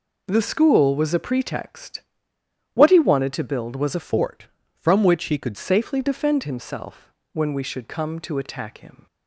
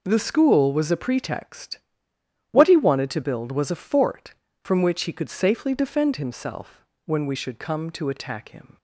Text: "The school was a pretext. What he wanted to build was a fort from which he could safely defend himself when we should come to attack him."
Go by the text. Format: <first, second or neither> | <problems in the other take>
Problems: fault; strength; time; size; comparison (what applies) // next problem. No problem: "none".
second | changes voice from "fort" to "could"; from 3.9 to 5.5 s; 1.6 s long // pauses between "himself" and "when"; slight; at 7.1 s; 0.20 s long; slight in the second